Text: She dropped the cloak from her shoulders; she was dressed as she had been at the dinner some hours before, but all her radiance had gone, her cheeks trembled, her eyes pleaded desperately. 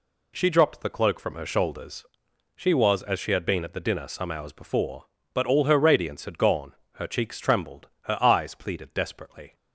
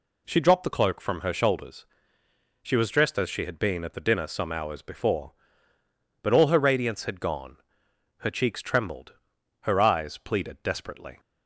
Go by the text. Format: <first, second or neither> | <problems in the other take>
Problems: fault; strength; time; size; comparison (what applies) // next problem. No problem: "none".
second | skips "dressed"; at 3.0 s